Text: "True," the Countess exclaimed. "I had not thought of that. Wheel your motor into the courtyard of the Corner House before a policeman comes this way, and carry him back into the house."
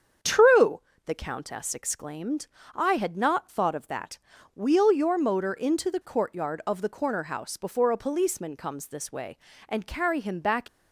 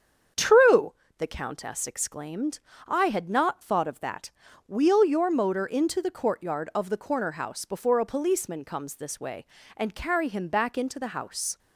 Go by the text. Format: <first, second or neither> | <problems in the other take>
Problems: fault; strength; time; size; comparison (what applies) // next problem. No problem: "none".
second | starts louder than the rest; strong; until 1.4 s; 7.5 dB; strong in the second // stops before "into the house"; at 10.6 s